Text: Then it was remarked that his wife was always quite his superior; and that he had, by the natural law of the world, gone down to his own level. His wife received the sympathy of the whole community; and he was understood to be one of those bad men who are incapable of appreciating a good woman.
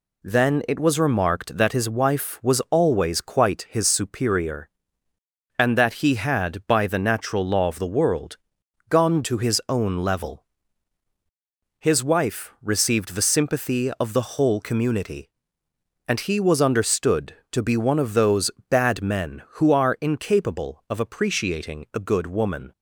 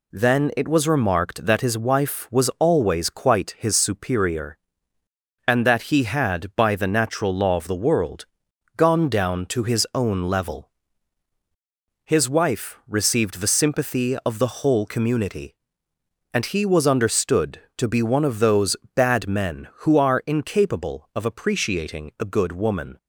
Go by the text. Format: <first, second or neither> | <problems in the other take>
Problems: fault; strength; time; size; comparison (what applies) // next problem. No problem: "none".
second | skips "down"; at 9.2 s // pauses between "those" and "bad"; slight; at 18.4 s; 0.20 s long; slight in the second